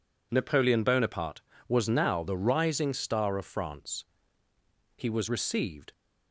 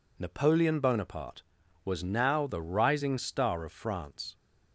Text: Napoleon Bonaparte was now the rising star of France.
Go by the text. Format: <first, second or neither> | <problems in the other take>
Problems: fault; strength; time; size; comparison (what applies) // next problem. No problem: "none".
second | goes on to say "He was received"; noticeable; from 4.9 s on; 0.94 s long